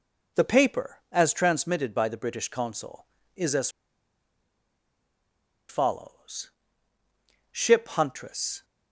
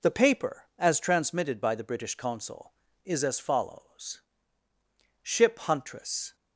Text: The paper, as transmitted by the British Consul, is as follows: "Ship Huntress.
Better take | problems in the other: second | pauses between "as" and "follows"; strong; at 3.6 s; 2.0 s long

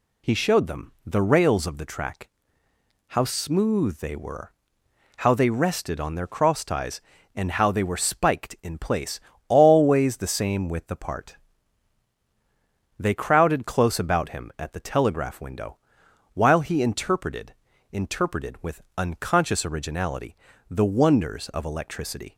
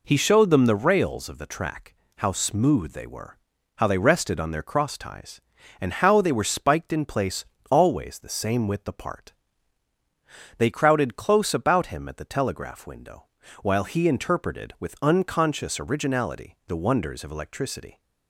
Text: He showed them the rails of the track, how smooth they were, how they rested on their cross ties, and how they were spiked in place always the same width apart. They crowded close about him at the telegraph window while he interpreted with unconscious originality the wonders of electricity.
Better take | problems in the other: second | pauses between "place" and "always"; slight; at 9.2 s; 0.28 s long; slight in the second // pauses between "window" and "while"; noticeable; at 15.7 s; 0.56 s long; slight in the second // says "interpreted" twice; at 17.9 s // pauses between "with" and "unconscious"; slight; at 18.8 s; 0.16 s long // pauses between "originality" and "the"; slight; at 20.3 s; 0.36 s long

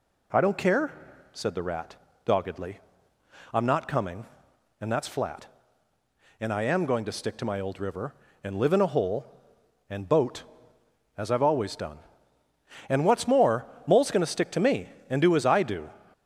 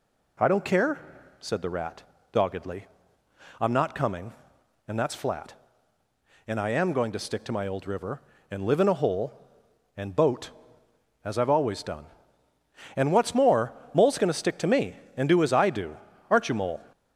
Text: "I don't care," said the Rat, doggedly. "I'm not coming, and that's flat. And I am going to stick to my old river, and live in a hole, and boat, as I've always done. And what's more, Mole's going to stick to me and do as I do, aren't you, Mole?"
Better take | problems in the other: second | stops before "aren't you Mole"; at 16.1 s

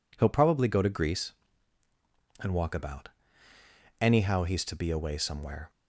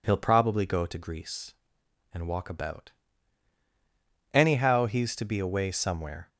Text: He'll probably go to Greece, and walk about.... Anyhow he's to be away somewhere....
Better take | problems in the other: neither | none

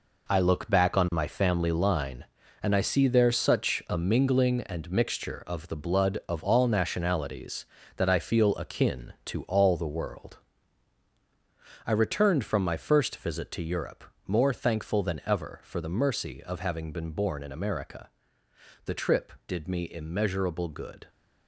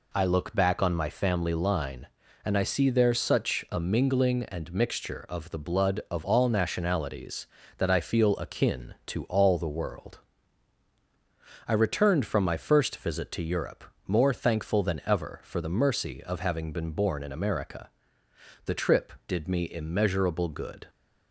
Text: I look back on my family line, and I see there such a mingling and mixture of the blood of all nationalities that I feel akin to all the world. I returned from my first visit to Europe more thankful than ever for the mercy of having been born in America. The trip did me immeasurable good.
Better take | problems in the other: second | gets quieter; strong; throughout; 9 dB // pauses between "Europe" and "more"; slight; at 14.0 s; 0.24 s long; slight in the second

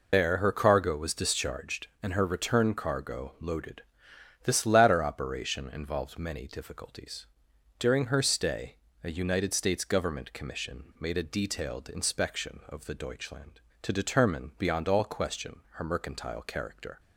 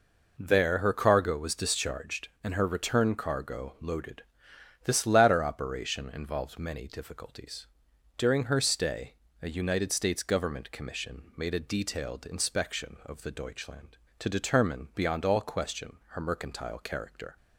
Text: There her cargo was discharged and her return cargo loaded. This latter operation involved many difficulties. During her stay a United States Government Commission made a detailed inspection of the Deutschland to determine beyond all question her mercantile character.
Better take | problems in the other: second | loses the start of "There"; at 0.1 s; 150 ms // pauses between "stay" and "a"; slight; at 8.7 s; 0.28 s long; slight in the second

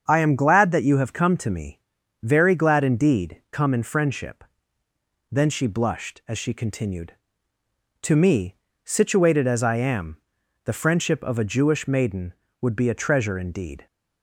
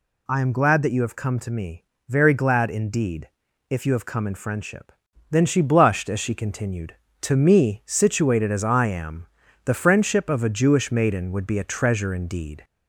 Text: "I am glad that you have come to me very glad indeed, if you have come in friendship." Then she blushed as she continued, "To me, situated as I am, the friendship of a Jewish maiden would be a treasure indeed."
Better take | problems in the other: second | starts louder than the rest; strong; until 1.0 s; 7.5 dB // pauses between "me" and "very"; at 1.7 s; 0.42 s long; slight in the second // skips "if you have"; at 3.4 s

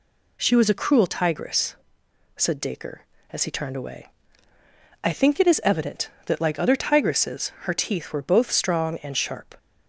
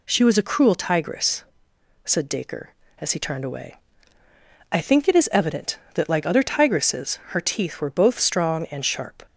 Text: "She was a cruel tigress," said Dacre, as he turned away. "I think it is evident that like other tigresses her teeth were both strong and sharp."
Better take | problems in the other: neither | none

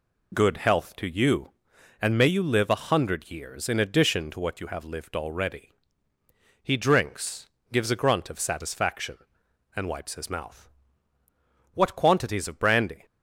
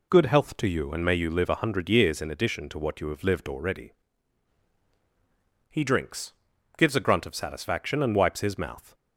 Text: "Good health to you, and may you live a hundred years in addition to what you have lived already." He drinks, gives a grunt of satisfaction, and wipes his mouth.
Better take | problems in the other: second | goes on to say "What quantities of brandy"; noticeable; from 11.7 s on; 1.2 s long

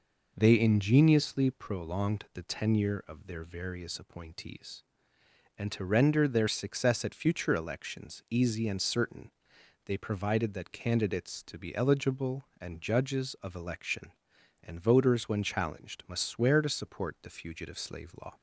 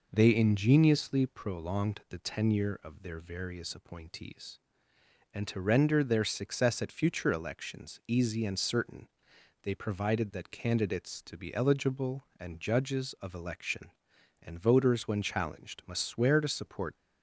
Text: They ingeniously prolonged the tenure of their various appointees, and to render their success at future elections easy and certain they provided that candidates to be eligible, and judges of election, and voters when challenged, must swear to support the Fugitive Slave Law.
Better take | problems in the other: first | pauses between "certain" and "they"; noticeable; at 9.0 s; 0.56 s long; noticeable in the first // stops before "the Fugitive Slave Law"; at 16.9 s

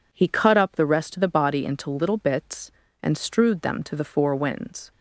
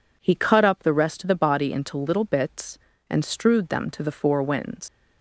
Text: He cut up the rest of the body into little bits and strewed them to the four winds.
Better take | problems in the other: first | leaves "winds" unfinished; at 4.8 s; 95 ms

